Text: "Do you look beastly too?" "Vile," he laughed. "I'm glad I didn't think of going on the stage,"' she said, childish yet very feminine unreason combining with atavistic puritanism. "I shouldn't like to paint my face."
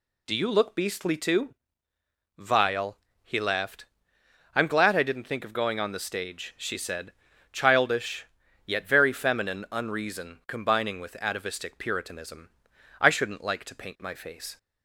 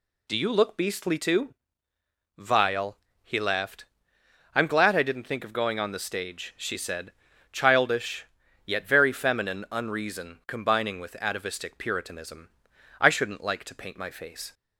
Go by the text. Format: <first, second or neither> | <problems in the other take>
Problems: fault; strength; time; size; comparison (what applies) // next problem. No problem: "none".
neither | pauses between "childish" and "yet"; the same in both